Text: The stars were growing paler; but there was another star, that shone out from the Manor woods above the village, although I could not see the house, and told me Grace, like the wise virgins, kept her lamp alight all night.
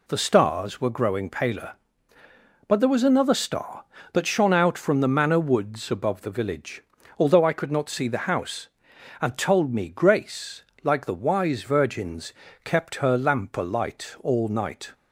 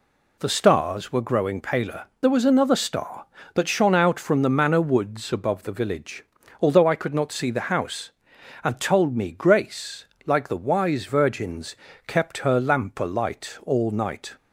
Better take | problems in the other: first | skips "but"; at 2.1 s

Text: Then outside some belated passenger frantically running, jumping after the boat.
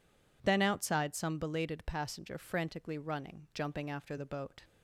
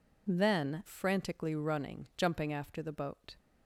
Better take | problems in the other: first | skips "outside some belated passenger"; at 0.8 s

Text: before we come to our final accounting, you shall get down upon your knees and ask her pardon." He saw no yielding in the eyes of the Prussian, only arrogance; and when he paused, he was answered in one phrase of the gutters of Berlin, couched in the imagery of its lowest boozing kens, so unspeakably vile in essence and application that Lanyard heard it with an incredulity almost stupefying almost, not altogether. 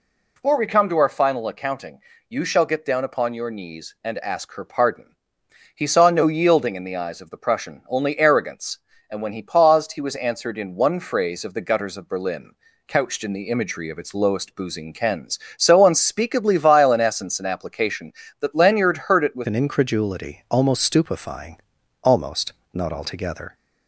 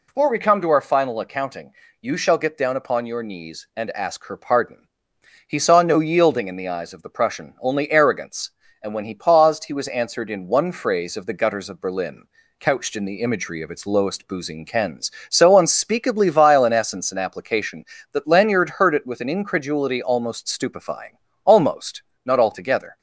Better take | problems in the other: second | changes voice at "an"; from 19.4 s on; 4.1 s long // pauses between "stupefying" and "almost"; noticeable; at 21.5 s; 0.46 s long; slight in the second

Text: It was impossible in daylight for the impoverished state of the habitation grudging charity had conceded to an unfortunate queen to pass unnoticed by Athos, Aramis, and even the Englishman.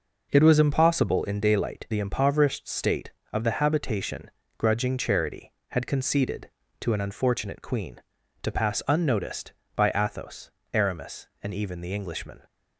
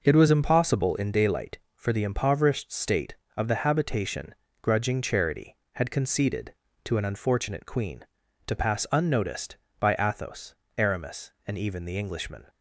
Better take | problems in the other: second | skips "for"; at 1.8 s // pauses between "habitation" and "grudging"; slight; at 4.3 s; 0.28 s long; slight in the second

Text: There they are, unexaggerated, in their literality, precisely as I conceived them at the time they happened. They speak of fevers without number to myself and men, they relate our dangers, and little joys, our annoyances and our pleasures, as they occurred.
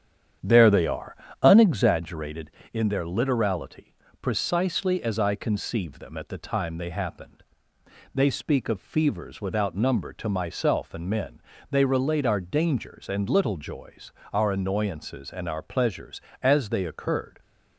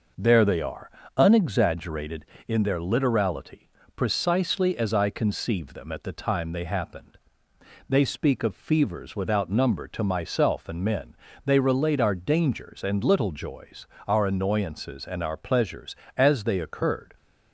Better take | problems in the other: second | starts louder than the rest; strong; until 2.0 s; 9 dB

